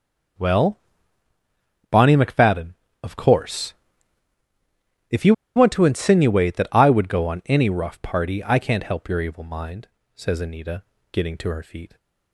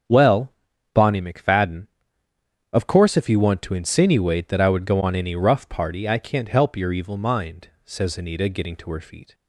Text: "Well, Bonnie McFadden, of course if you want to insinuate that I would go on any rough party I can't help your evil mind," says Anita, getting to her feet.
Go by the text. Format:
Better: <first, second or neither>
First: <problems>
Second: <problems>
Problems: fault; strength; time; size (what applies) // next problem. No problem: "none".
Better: second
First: starts louder than the rest; until 2.5 s; 6.5 dB // pauses between "course" and "if"; strong; at 3.7 s; 1.3 s long // pauses between "you" and "want"; slight; at 5.3 s; 0.22 s long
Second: starts louder than the rest; until 1.4 s; 7 dB